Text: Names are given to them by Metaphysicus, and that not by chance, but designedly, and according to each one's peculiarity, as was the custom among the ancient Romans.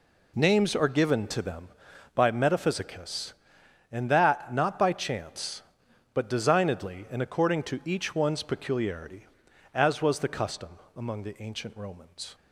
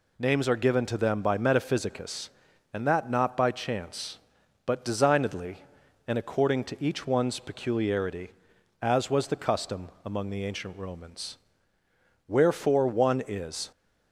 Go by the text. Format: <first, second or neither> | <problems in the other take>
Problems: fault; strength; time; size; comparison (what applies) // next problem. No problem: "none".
first | pauses between "custom" and "among"; slight; at 9.8 s; 0.16 s long; slight in the first // goes on to say "Wherefore one is"; from 12.2 s on; 1.4 s long